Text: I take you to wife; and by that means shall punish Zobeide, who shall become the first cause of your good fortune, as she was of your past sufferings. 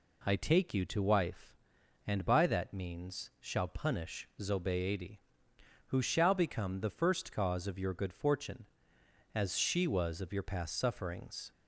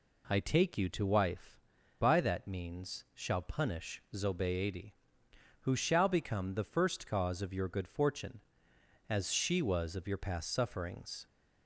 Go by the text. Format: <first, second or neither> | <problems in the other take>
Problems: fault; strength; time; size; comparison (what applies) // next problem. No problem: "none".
first | skips "and"; at 1.8 s